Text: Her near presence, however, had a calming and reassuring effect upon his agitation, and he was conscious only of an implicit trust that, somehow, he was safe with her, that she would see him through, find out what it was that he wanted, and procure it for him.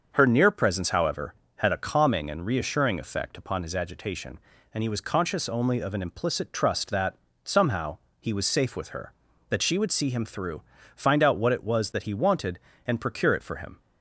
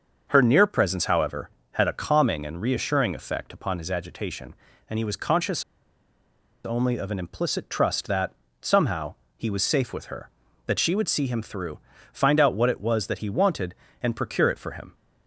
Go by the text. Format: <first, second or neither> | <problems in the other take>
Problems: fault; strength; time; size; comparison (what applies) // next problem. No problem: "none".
first | starts louder than the rest; until 1.3 s; 6.5 dB; also in the first // pauses between "conscious" and "only"; at 5.6 s; 1.0 s long